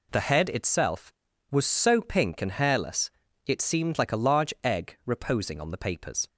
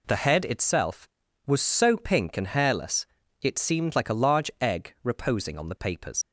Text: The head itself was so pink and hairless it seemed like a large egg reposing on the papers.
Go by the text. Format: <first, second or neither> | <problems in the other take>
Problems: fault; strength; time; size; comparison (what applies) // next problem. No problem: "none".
first | pauses between "hairless" and "it"; slight; at 3.0 s; 0.34 s long; slight in the first // leaves "papers" unfinished; at 6.2 s; 60 ms